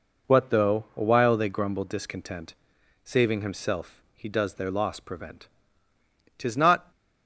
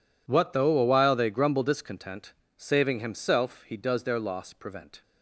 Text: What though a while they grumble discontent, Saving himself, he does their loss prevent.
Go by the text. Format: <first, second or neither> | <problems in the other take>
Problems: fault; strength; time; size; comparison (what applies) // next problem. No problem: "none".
second | goes on to say "Tis not"; from 6.3 s on; 0.52 s long